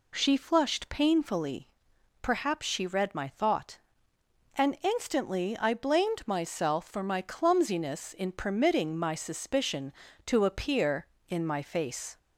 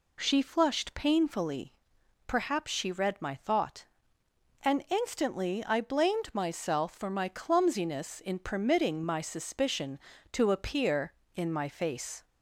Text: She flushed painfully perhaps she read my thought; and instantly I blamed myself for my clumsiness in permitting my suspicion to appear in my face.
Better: neither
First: pauses between "painfully" and "perhaps"; noticeable; at 1.6 s; 0.54 s long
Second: pauses between "painfully" and "perhaps"; noticeable; at 1.7 s; 0.54 s long

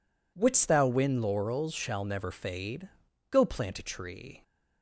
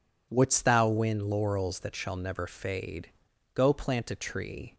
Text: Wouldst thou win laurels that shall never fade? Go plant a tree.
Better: second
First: skips "that"; at 1.7 s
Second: none

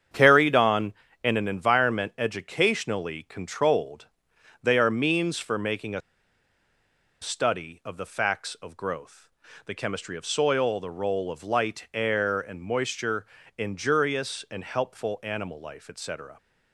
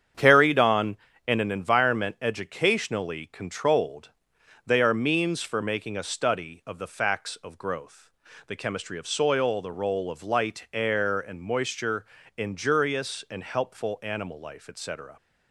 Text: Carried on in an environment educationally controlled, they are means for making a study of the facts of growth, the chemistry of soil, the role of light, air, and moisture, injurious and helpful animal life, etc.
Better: second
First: starts louder than the rest; strong; until 1.4 s; 8 dB // pauses between "a" and "study"; at 6.0 s; 1.2 s long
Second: starts louder than the rest; strong; until 1.4 s; 8 dB

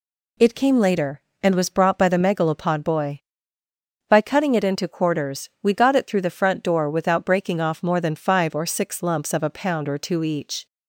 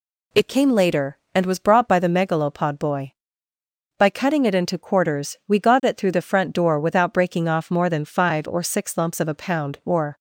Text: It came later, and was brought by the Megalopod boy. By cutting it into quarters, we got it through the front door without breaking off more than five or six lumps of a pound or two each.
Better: first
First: none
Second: stops before "two each"; at 10.1 s

